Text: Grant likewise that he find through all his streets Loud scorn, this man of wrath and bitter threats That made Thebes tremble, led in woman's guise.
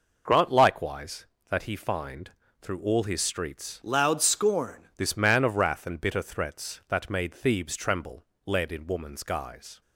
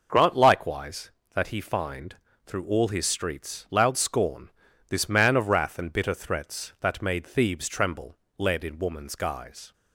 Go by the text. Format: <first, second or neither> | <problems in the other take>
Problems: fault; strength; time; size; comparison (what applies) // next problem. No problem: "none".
second | pauses between "find" and "through"; slight; at 2.3 s; 0.28 s long; slight in the second // changes voice from "Loud" to "scorn"; from 3.8 to 4.8 s; 1.0 s long